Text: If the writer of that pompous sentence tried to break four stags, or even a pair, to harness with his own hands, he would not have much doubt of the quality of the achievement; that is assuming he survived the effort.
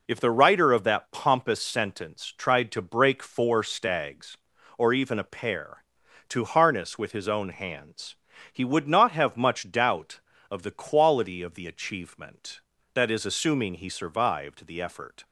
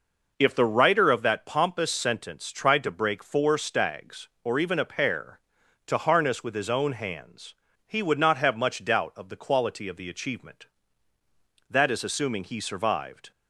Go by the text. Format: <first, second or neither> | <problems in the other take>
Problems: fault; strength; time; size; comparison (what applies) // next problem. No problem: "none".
first | stops before "the effort"; at 13.3 s